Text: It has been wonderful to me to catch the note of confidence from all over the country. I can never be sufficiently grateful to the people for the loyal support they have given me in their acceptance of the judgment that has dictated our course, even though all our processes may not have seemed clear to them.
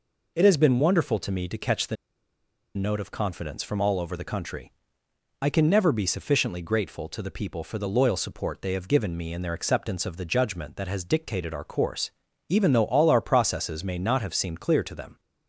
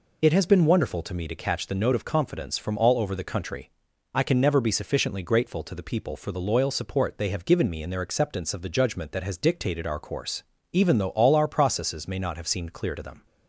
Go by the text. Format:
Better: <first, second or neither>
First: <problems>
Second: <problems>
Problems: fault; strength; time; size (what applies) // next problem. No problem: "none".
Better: second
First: pauses between "the" and "note"; noticeable; at 1.9 s; 0.79 s long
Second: none